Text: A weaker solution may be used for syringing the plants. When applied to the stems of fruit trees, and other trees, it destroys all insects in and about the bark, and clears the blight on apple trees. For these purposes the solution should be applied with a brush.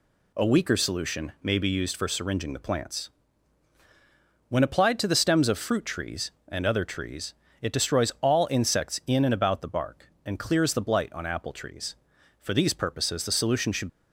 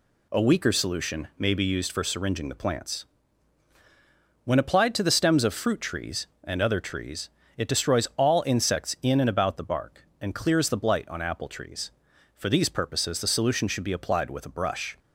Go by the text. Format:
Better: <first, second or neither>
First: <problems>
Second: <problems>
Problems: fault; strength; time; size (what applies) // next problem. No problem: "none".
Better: second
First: stops before "be applied with a brush"; at 13.8 s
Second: none